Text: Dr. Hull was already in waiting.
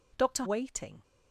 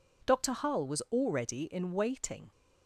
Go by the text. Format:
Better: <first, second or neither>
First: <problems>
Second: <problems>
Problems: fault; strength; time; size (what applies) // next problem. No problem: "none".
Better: second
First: skips "Hull was already in"; at 0.4 s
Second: none